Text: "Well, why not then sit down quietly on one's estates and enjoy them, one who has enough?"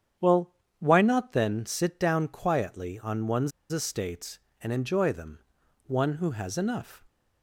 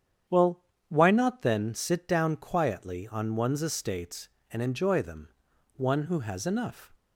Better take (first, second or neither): second